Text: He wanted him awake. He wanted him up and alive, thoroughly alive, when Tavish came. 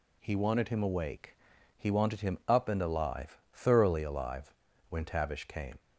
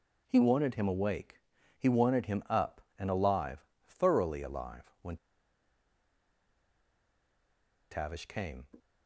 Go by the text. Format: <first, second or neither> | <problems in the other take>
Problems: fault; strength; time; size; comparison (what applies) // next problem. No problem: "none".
first | pauses between "when" and "Tavish"; strong; at 5.1 s; 2.7 s long